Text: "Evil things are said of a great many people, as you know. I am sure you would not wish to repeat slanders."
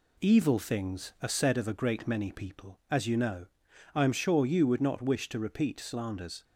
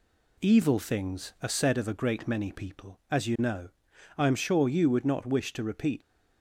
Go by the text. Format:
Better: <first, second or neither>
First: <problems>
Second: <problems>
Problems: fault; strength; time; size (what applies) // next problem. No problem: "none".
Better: first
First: none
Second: stops before "slanders"; at 6.0 s